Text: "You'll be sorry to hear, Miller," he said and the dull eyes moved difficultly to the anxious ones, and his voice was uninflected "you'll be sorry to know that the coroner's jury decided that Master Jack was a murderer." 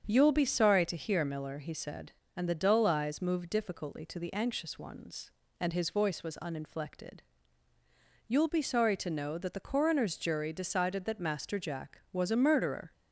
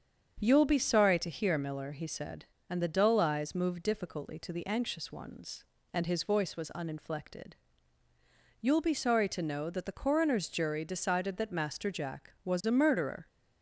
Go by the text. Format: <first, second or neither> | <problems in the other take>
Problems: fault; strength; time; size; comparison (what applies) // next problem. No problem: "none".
neither | starts louder than the rest; strong; the same in both // pauses between "uninflected" and "you'll"; the same in both